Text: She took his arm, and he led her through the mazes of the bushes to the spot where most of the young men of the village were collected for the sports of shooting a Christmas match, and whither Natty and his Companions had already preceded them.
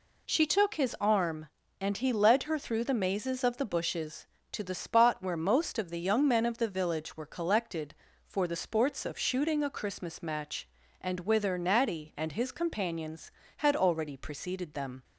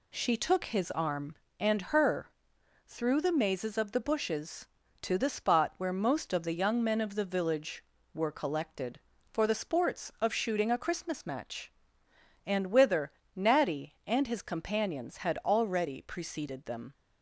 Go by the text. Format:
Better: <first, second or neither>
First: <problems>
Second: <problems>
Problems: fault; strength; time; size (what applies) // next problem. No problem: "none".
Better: first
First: none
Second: skips "he led"; at 1.8 s // pauses between "her" and "through"; noticeable; at 2.2 s; 0.56 s long // pauses between "whither" and "Natty"; slight; at 13.1 s; 0.24 s long